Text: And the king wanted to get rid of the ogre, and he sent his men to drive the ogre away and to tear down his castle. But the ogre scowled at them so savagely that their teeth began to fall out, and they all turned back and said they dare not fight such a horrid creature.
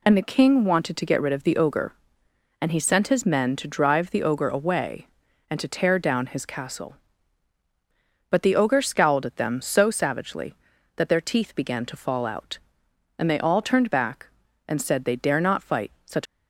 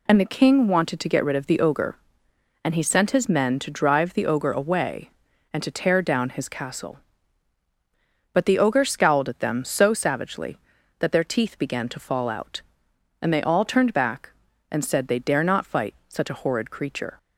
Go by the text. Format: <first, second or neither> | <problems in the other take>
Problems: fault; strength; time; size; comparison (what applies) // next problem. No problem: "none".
second | stops before "a horrid creature"; at 16.2 s